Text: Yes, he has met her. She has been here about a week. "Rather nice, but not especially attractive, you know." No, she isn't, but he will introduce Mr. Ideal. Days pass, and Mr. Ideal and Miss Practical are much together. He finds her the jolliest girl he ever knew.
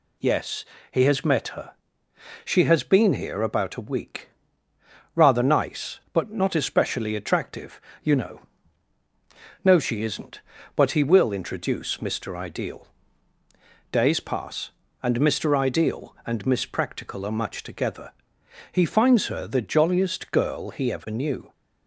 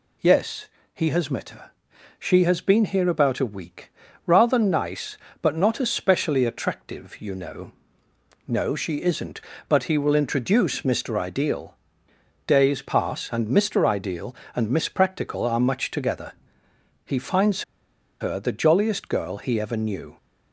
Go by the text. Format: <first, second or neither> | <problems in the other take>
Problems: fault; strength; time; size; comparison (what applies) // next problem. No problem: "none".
first | pauses between "finds" and "her"; noticeable; at 17.6 s; 0.57 s long